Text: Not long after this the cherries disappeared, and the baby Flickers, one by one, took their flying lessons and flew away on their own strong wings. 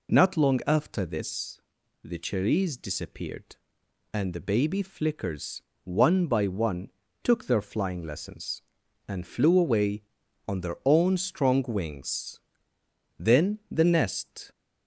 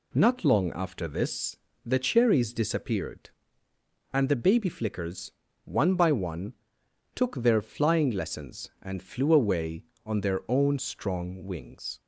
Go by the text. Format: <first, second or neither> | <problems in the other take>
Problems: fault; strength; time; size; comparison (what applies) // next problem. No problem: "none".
second | pauses between "this" and "the"; at 1.6 s; 0.42 s long; slight in the second // goes on to say "Then the nest"; noticeable; from 13.2 s on; 1.3 s long